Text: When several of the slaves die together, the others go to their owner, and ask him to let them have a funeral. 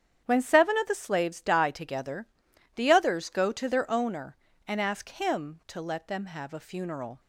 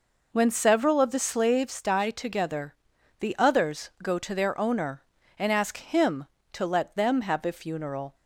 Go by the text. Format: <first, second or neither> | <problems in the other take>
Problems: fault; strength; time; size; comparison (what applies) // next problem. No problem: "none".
second | starts louder than the rest; strong; until 1.2 s; 9 dB // says "seven" for "several"; at 0.3 s